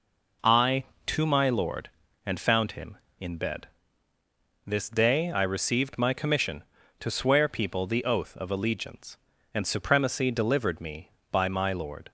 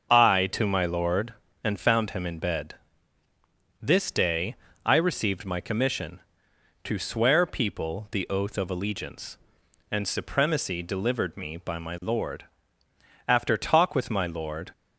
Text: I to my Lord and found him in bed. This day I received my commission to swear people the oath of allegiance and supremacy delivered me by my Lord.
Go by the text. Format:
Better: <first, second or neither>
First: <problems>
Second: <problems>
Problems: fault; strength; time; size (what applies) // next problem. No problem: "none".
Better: first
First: none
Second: starts louder than the rest; until 1.1 s; 6.5 dB // pauses between "day" and "I"; slight; at 4.5 s; 0.30 s long // goes on to say "After talk with my Lord"; from 13.2 s on; 1.4 s long